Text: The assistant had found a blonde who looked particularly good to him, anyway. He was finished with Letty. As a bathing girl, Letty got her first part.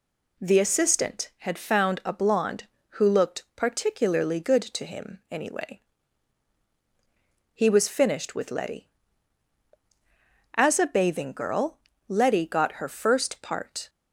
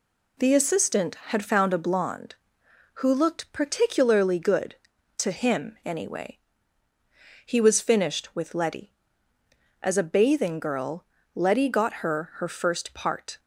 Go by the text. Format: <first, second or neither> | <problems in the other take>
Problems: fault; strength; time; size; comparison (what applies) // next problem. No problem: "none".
first | says "her" twice; at 12.3 s